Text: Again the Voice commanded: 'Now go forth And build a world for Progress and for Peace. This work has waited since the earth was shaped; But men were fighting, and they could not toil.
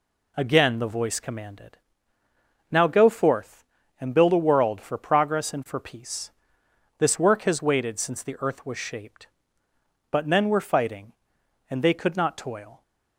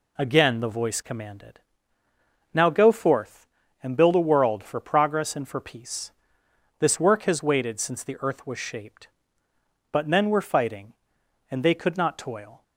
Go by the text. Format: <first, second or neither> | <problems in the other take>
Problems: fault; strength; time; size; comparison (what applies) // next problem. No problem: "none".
neither | none